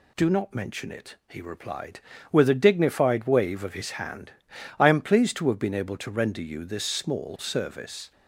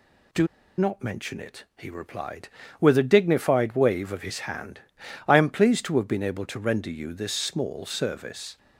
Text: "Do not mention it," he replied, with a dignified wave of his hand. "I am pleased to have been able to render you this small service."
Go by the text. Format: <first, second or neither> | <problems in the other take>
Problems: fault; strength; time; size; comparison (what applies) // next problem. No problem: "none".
first | pauses between "Do" and "not"; slight; at 0.4 s; 0.30 s long